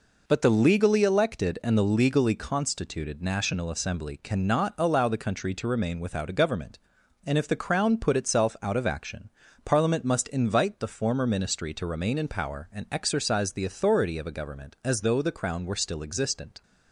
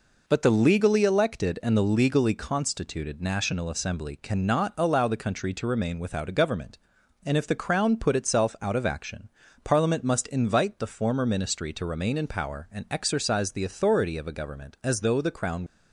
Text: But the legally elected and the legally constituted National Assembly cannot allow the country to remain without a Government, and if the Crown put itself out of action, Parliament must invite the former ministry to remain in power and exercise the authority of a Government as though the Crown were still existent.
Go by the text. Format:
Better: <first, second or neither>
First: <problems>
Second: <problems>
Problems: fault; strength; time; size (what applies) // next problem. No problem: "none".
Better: first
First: none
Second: stops before "were still existent"; at 15.6 s